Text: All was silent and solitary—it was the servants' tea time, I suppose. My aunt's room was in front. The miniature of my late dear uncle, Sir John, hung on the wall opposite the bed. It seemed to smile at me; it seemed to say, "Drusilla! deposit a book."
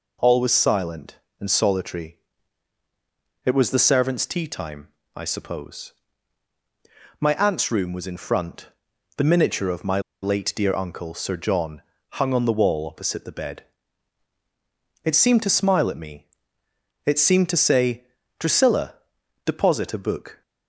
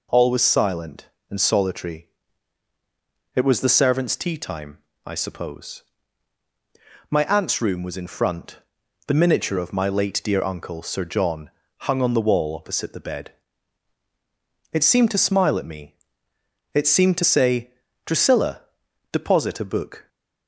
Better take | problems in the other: second | pauses between "my" and "late"; slight; at 9.9 s; 0.23 s long

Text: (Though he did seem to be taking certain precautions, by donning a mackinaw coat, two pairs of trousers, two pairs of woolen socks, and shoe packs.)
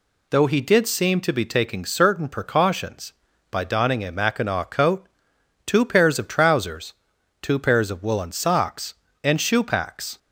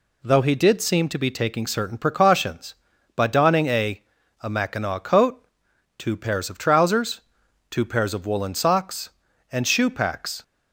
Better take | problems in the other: first | says "a" twice; at 4.4 s

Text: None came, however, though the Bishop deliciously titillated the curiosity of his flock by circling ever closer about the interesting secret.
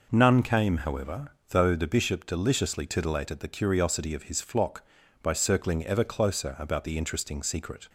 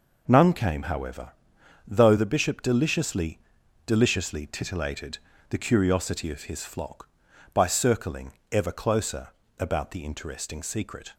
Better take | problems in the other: first | says "deliciously" twice; at 3.8 s // pauses between "titillated" and "the"; slight; at 5.1 s; 0.30 s long // pauses between "circling" and "ever"; slight; at 8.3 s; 0.18 s long // pauses between "closer" and "about"; slight; at 9.2 s; 0.30 s long

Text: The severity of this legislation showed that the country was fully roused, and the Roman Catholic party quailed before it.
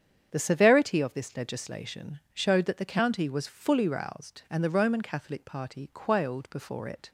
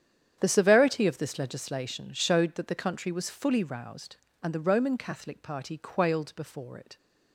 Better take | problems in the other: second | starts louder than the rest; strong; until 1.3 s; 8 dB; strong in the second // says "county" for "country"; at 2.8 s

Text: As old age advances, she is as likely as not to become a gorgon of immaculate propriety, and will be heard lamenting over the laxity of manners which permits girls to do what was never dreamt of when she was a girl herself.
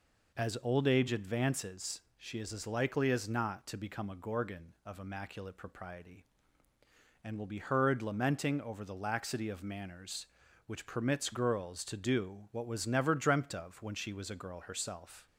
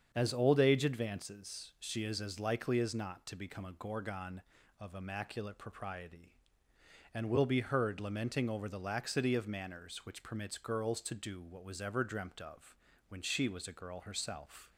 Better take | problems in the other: first | starts louder than the rest; strong; until 1.1 s; 7 dB // says "ever" for "never"; at 11.7 s // pauses between "of" and "when"; slight; at 12.7 s; 0.32 s long

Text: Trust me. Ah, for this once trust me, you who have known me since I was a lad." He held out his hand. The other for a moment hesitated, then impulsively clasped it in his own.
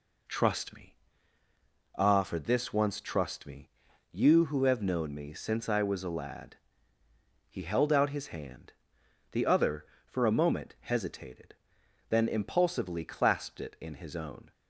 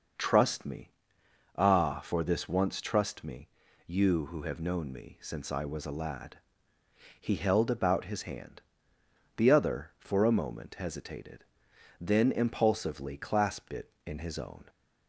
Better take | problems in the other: first | starts louder than the rest; noticeable; until 1.8 s; 6 dB // says "about" for "out"; at 7.7 s

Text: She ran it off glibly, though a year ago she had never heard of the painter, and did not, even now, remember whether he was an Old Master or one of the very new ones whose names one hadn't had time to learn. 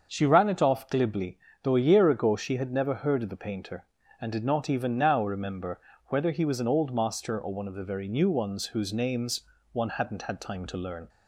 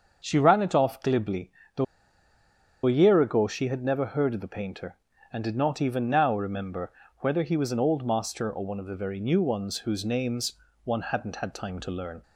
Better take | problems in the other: first | starts louder than the rest; until 1.2 s; 6.5 dB; also in the first // pauses between "though" and "a"; at 1.8 s; 1.0 s long // pauses between "remember" and "whether"; slight; at 6.9 s; 0.28 s long; slight in the first // pauses between "names" and "one"; slight; at 10.5 s; 0.30 s long; slight in the first

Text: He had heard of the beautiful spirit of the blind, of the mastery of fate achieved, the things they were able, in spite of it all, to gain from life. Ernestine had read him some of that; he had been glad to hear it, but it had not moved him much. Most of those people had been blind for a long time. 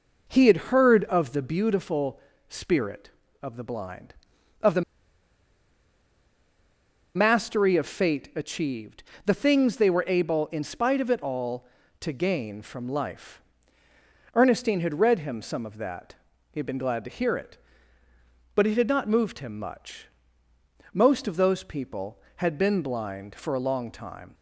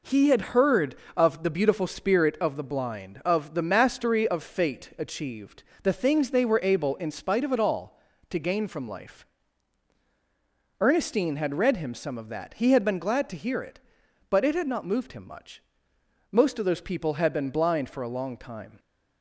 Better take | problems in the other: second | pauses between "beautiful" and "spirit"; slight; at 2.1 s; 0.28 s long // pauses between "the" and "mastery"; strong; at 4.8 s; 2.3 s long

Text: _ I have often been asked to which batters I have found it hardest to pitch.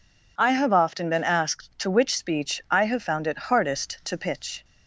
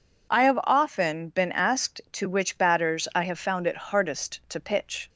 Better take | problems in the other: second | says "speech" for "batters"; at 2.1 s

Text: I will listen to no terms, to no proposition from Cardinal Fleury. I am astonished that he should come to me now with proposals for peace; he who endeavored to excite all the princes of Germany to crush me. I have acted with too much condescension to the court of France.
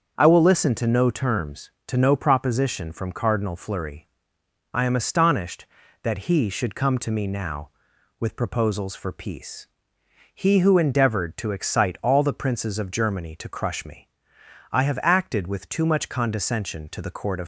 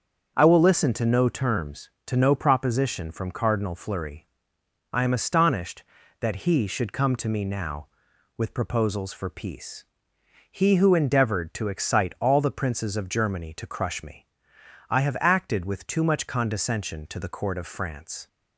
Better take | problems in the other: second | starts louder than the rest; until 1.2 s; 6.5 dB; also in the second // stops before "France"; at 17.4 s

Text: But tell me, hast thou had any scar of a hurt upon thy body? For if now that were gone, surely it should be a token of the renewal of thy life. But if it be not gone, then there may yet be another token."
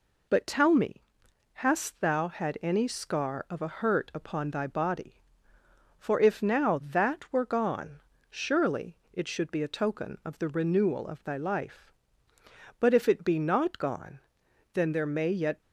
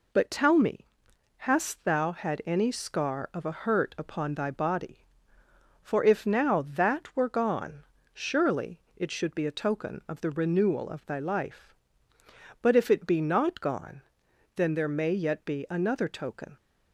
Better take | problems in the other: second | pauses between "surely" and "it"; slight; at 8.9 s; 0.20 s long; slight in the second // stops before "be another token"; at 15.6 s

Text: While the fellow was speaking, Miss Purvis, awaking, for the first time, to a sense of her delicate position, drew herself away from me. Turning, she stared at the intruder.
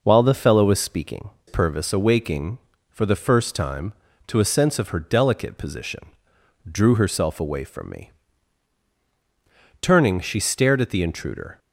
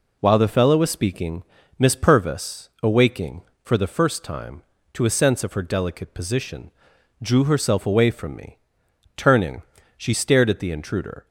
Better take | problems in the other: second | skips "Miss"; at 1.3 s

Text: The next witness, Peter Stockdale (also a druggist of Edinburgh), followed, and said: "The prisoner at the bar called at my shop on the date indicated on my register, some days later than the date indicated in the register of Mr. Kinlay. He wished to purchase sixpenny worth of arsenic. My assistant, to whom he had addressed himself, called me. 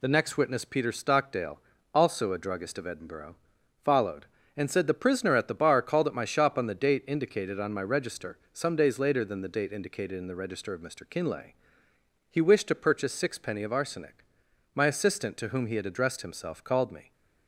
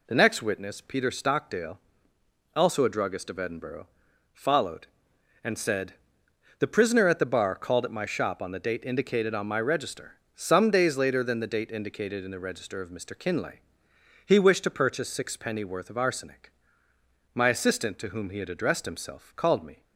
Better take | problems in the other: second | skips "worth"; at 13.6 s

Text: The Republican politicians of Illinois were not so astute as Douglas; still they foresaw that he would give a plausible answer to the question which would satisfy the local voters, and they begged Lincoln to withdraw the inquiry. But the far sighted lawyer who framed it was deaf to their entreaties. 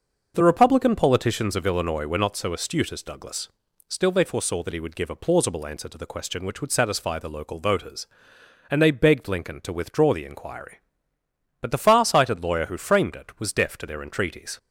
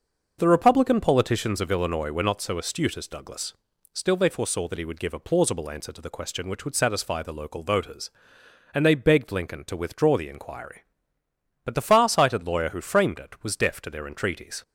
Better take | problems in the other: neither | starts louder than the rest; noticeable; the same in both

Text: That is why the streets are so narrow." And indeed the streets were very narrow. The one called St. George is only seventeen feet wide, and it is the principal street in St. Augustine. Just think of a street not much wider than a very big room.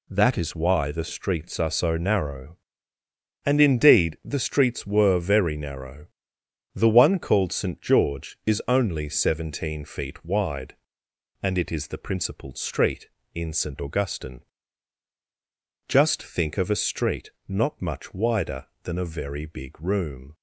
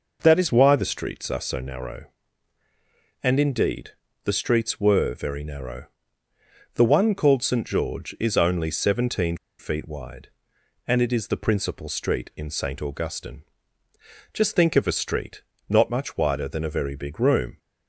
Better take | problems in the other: first | pauses between "indeed" and "the"; slight; at 3.9 s; 0.34 s long // pauses between "seventeen" and "feet"; slight; at 9.3 s; 0.24 s long // pauses between "street" and "not"; slight; at 15.4 s; 0.26 s long; slight in the first

